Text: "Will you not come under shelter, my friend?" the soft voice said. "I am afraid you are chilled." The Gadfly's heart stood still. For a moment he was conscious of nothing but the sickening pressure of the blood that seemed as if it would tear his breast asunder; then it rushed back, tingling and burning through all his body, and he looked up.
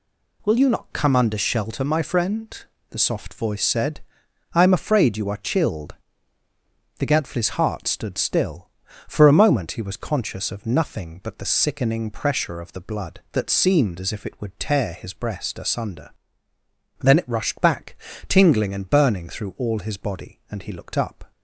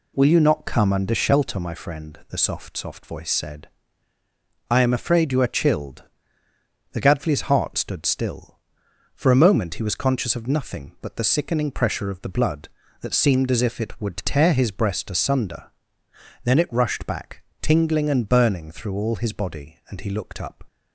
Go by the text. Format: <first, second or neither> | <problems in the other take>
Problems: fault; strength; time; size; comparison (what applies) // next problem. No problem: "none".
first | says "soft" twice; at 2.7 s